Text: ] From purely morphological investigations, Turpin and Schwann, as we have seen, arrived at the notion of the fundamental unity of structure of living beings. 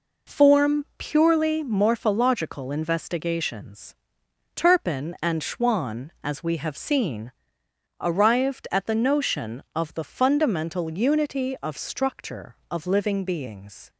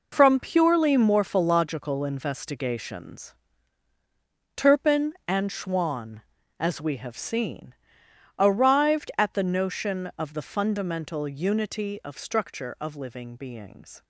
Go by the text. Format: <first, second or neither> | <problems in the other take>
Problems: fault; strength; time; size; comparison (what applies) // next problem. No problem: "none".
second | says "Form" for "From"; at 0.2 s